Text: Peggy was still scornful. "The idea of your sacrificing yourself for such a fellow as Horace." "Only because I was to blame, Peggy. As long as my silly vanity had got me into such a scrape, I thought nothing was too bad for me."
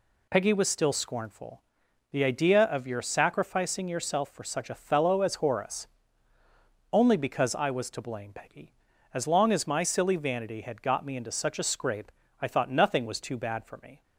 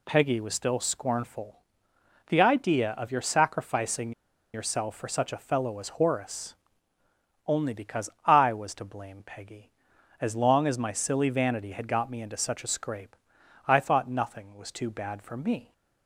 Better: first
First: none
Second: pauses between "sacrificing" and "yourself"; at 4.1 s; 0.41 s long // pauses between "because" and "I"; slight; at 8.1 s; 0.16 s long

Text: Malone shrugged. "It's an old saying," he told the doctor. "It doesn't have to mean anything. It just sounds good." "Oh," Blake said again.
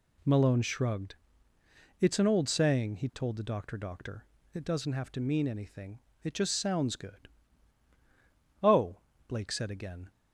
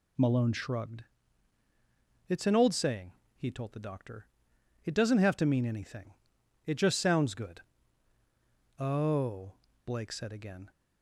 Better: second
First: says "doctor" twice; at 3.7 s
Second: none

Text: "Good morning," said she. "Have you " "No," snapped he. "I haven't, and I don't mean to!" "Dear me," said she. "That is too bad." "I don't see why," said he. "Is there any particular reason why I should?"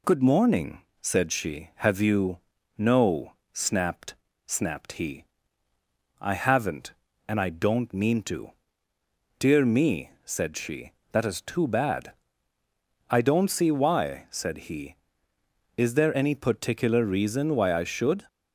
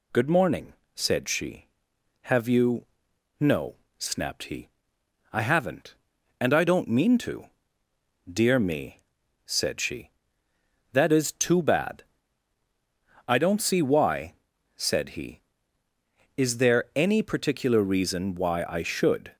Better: second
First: says "snapped" twice; at 4.4 s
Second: none

